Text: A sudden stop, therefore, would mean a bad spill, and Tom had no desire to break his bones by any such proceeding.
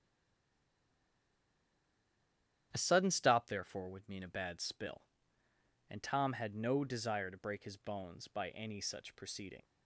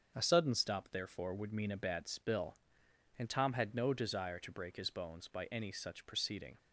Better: second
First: stays silent before the first word; strong; until 2.7 s; 2.7 s long // starts louder than the rest; strong; until 3.7 s; 10 dB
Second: starts louder than the rest; until 1.1 s; 6.5 dB

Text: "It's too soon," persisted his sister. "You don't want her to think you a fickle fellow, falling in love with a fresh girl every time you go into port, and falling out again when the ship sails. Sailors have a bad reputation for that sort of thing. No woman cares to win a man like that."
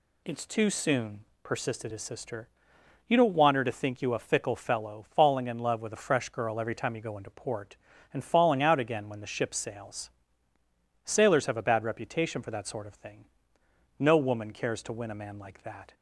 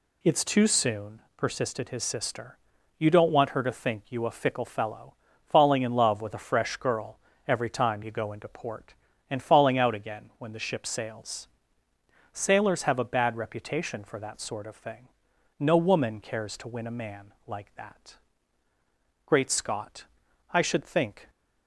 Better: first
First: none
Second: pauses between "girl" and "every"; slight; at 7.1 s; 0.28 s long // goes on to say "Great Scott I should think"; strong; from 19.2 s on; 2.0 s long

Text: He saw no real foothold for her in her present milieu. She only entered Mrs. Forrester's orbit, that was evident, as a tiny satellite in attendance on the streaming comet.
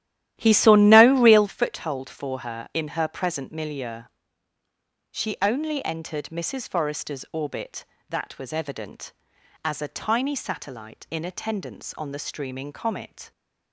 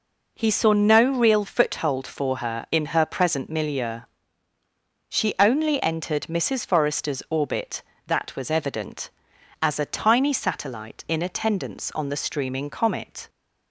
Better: second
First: starts louder than the rest; strong; until 1.6 s; 12.5 dB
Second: none

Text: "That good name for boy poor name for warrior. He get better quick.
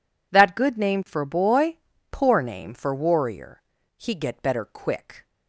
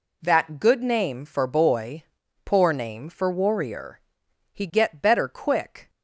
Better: neither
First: pauses between "boy" and "poor"; slight; at 1.7 s; 0.34 s long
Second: pauses between "boy" and "poor"; at 2.0 s; 0.42 s long

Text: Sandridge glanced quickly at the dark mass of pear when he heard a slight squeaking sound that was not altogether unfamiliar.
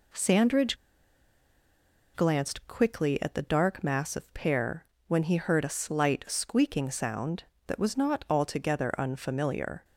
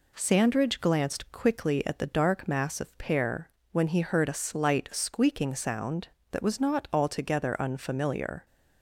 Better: second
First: pauses between "Sandridge" and "glanced"; strong; at 0.7 s; 1.3 s long // pauses between "pear" and "when"; slight; at 4.8 s; 0.24 s long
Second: pauses between "pear" and "when"; slight; at 3.4 s; 0.24 s long

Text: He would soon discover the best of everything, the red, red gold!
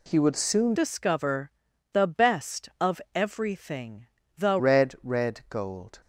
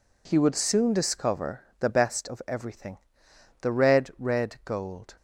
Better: second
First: changes voice from "discover" to "the"; from 0.7 to 4.5 s; 3.8 s long // pauses between "discover" and "the"; at 1.5 s; 0.42 s long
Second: pauses between "discover" and "the"; slight; at 1.6 s; 0.18 s long

